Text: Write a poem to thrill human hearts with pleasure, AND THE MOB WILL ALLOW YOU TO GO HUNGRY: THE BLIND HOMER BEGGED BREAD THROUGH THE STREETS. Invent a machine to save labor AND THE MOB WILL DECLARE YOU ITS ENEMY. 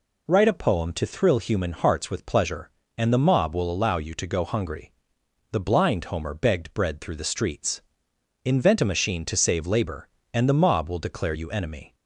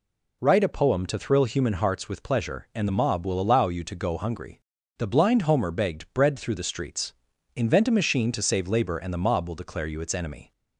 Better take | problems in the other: second | skips "ITS"; at 11.5 s

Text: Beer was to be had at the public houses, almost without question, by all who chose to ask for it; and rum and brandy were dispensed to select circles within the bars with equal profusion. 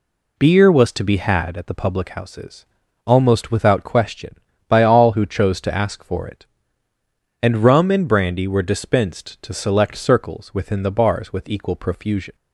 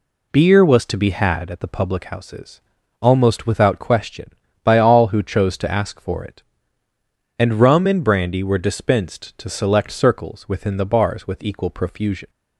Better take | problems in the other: neither | none

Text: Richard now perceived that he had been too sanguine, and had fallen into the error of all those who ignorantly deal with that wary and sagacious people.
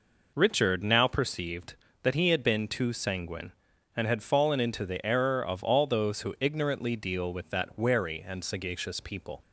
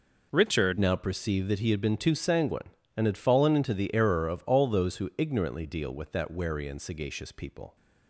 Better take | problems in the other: first | changes voice at "now"; from 0.7 s on; 7.0 s long

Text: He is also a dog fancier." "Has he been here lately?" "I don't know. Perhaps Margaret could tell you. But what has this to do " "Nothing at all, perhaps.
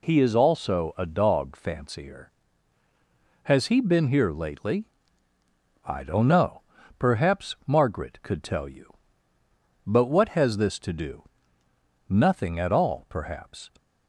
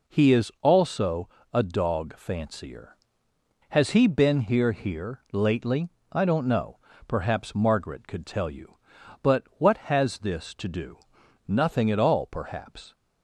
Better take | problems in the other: first | pauses between "also" and "a"; slight; at 1.2 s; 0.24 s long // says "here" twice; at 4.7 s // pauses between "But" and "what"; slight; at 9.4 s; 0.16 s long

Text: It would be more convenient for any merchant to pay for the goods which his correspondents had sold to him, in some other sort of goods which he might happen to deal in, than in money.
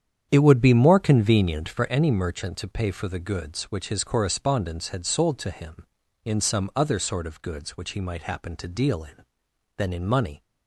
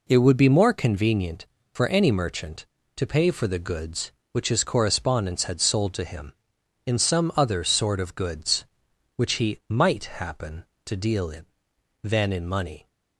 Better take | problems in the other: second | starts louder than the rest; strong; until 2.0 s; 8.5 dB

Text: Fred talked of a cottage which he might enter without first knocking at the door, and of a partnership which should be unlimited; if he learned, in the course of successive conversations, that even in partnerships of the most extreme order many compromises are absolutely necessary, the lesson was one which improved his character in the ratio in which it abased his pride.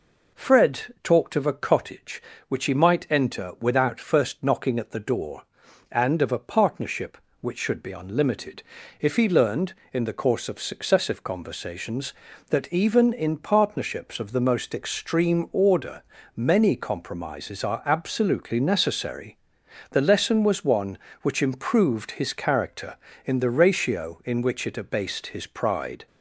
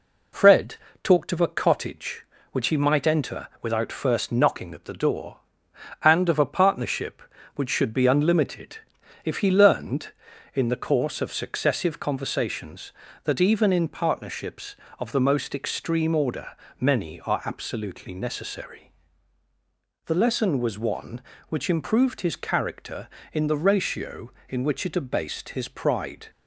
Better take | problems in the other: first | pauses between "Fred" and "talked"; slight; at 0.7 s; 0.30 s long // pauses between "enter" and "without"; slight; at 3.4 s; 0.16 s long // pauses between "order" and "many"; slight; at 16.4 s; 0.32 s long; slight in the first // skips "compromises"; at 17.1 s

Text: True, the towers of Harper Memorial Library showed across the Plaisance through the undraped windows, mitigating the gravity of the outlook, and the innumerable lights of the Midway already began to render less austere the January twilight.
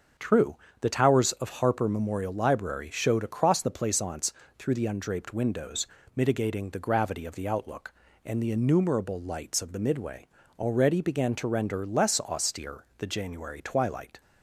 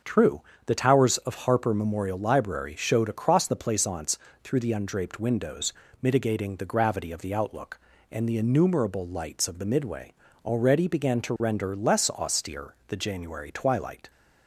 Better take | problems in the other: neither | starts louder than the rest; the same in both // pauses between "Plaisance" and "through"; slight; the same in both // pauses between "Midway" and "already"; slight; the same in both

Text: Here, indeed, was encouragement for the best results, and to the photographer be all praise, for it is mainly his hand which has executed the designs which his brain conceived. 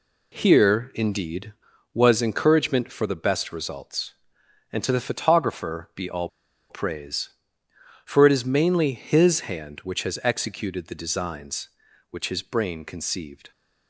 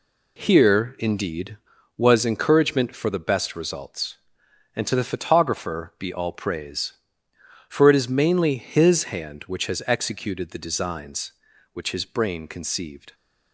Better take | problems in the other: second | pauses between "all" and "praise"; at 6.2 s; 0.42 s long

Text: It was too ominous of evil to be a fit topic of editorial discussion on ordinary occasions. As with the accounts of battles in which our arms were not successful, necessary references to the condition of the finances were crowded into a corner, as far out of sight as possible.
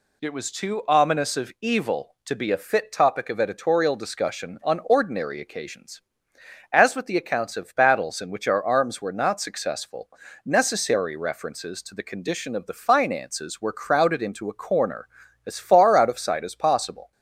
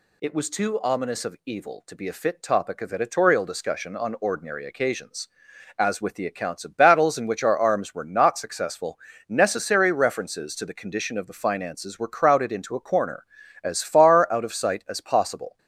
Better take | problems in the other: neither | none

